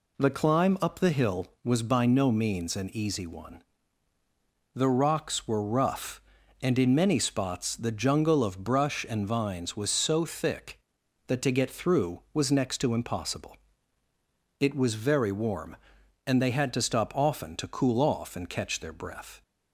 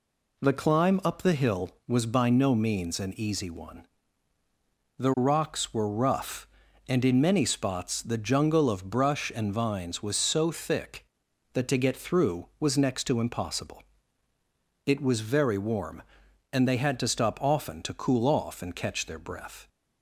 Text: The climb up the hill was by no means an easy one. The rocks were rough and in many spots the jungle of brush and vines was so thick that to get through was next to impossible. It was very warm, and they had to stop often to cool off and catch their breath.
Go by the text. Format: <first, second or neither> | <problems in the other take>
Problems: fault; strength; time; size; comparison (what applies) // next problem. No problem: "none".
neither | none